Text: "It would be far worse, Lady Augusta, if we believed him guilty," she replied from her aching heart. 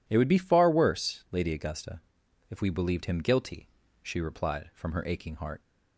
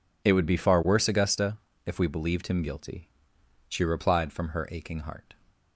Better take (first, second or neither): first